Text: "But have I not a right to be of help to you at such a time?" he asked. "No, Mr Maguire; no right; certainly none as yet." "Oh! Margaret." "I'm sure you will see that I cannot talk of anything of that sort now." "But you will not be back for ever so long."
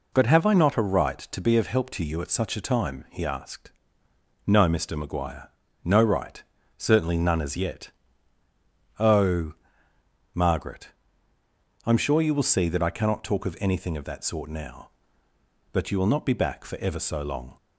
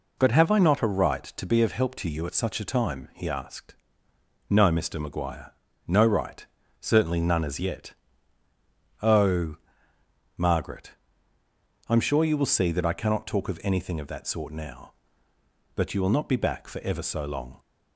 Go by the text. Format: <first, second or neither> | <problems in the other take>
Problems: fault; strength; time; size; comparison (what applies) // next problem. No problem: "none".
neither | none